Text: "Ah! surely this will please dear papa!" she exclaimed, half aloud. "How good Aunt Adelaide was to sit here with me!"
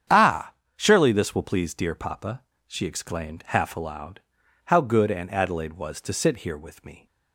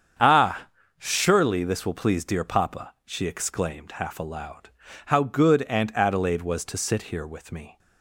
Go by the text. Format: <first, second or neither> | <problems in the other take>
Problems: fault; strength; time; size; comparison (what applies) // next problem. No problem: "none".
neither | starts louder than the rest; strong; the same in both